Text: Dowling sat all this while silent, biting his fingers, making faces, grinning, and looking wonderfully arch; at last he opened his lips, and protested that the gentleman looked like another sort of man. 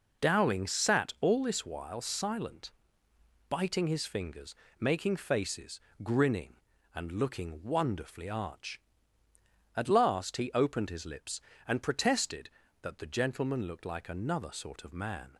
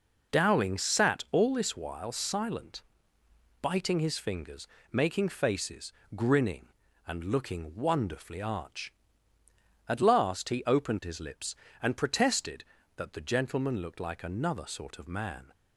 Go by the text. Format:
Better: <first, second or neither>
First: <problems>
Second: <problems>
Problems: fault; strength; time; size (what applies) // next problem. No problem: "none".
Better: neither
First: none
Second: none